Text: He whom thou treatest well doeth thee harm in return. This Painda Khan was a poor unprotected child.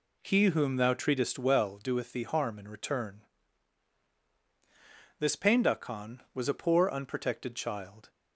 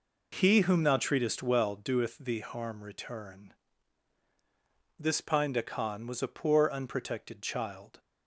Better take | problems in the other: first | skips "in"; at 2.8 s

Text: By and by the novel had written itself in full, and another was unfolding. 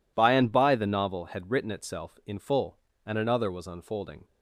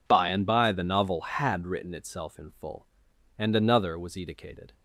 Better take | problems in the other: first | says "edicated" for "unfolding"; at 4.1 s

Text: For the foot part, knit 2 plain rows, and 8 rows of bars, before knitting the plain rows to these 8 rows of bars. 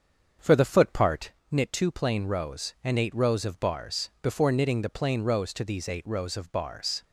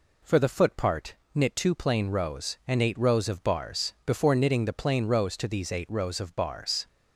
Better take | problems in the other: second | starts louder than the rest; until 1.4 s; 7 dB

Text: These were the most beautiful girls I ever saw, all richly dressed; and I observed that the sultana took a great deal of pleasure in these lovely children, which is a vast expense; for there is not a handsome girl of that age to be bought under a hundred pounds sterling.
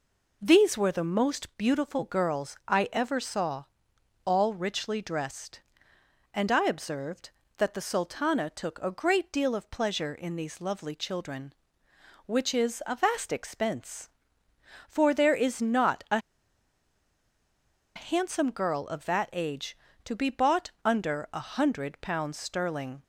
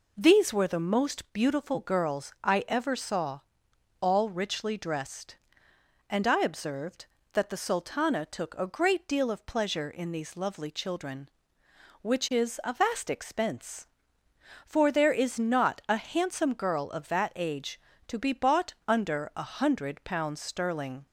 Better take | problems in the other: second | pauses between "a" and "handsome"; strong; at 16.1 s; 1.7 s long

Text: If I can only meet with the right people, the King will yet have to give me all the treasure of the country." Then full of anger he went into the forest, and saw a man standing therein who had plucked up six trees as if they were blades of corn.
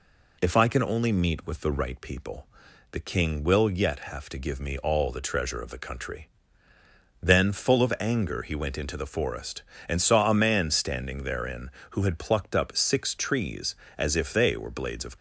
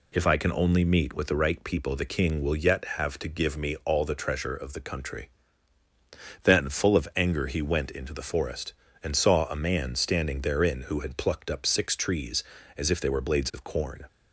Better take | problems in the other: second | stops before "corn"; at 15.1 s

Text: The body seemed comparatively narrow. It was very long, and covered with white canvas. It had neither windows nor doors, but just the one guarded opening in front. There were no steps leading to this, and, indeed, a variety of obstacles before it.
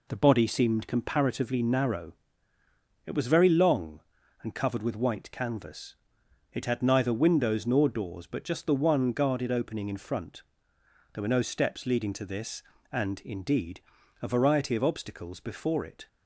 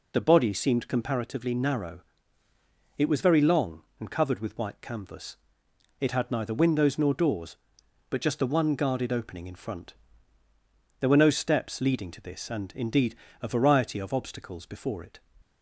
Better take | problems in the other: neither | none

